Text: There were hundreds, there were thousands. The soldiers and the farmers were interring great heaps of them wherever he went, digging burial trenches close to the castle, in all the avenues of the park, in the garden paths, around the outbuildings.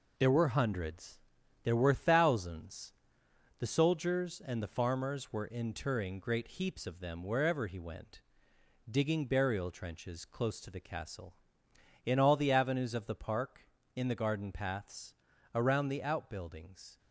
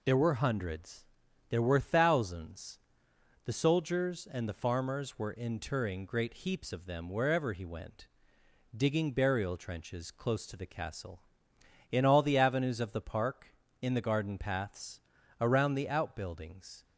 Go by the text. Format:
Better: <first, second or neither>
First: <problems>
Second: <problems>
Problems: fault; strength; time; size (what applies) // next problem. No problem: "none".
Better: second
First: gets quieter; noticeable; throughout; 6 dB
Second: none